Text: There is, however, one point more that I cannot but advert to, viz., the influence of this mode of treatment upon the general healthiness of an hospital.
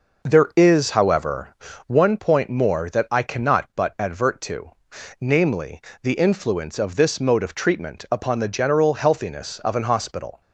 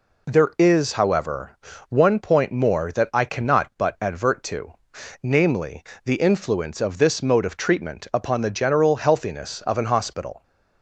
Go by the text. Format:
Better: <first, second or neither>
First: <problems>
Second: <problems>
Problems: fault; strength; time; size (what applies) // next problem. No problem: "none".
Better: second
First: starts louder than the rest; noticeable; until 1.9 s; 5.5 dB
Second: none